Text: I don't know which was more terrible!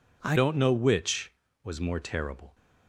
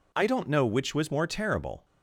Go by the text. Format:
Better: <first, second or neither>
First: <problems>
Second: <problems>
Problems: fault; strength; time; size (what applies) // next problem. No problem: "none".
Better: second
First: changes voice at "don't"; from 0.3 s on; 2.2 s long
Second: none